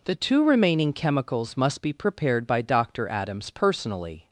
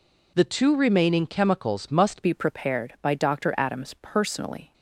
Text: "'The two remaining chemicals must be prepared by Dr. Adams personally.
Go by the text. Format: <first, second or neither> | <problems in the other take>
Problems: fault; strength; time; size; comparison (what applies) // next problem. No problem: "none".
first | changes voice at "be"; from 2.2 s on; 2.5 s long